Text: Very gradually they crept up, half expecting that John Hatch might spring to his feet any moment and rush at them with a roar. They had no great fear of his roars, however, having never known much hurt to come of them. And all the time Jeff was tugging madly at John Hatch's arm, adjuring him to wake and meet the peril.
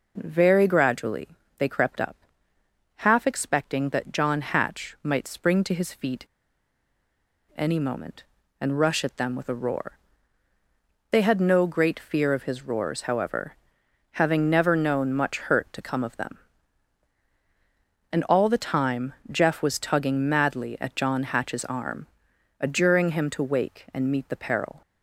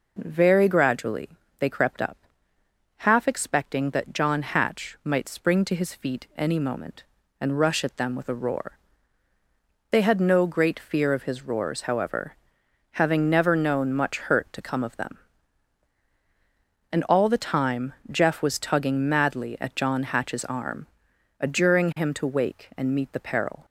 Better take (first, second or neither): second